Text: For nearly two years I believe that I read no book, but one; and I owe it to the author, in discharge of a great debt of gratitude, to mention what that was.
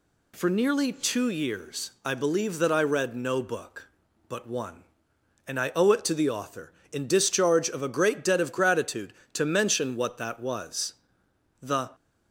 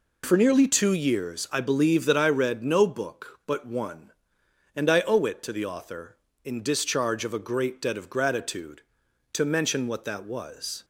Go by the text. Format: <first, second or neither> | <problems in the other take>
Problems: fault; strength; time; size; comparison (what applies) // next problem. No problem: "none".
second | goes on to say "The"; slight; from 11.6 s on; 0.28 s long